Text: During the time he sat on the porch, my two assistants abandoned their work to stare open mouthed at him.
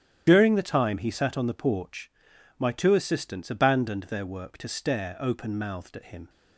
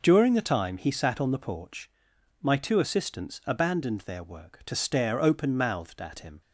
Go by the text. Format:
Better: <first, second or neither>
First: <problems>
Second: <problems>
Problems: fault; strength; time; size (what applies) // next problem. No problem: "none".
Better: second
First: loses the start of "During"; at 0.2 s; 80 ms // starts louder than the rest; strong; until 1.2 s; 11 dB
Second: none